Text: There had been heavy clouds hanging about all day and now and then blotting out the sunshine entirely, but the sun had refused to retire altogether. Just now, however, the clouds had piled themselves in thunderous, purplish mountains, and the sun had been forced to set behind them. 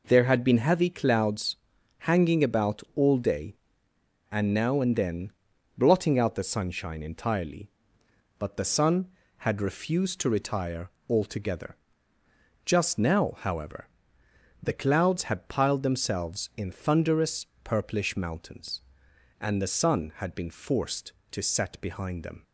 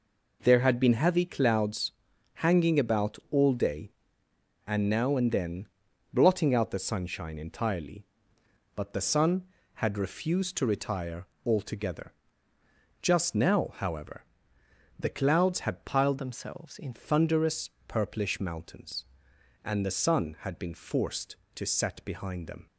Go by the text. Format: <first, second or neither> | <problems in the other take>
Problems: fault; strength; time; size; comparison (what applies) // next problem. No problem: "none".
first | pauses between "clouds" and "hanging"; at 1.9 s; 0.44 s long; also in the first // pauses between "then" and "blotting"; noticeable; at 5.6 s; 0.46 s long; noticeable in the first // pauses between "retire" and "altogether"; slight; at 11.2 s; 0.20 s long; slight in the first // changes voice from "themselves" to "in"; from 16.1 to 16.9 s; 0.8 s long